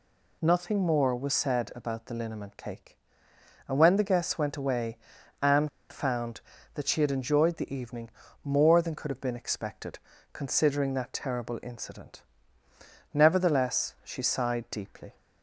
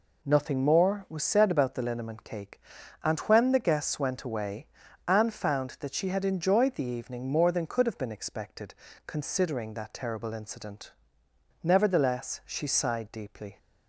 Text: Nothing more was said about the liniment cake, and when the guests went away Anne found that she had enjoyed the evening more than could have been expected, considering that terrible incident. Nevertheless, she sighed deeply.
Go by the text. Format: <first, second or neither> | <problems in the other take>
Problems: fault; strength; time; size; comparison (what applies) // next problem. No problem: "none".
second | pauses between "away" and "Anne"; at 4.9 s; 0.44 s long; also in the second // pauses between "Anne" and "found"; slight; at 5.6 s; 0.20 s long // pauses between "evening" and "more"; slight; at 8.0 s; 0.34 s long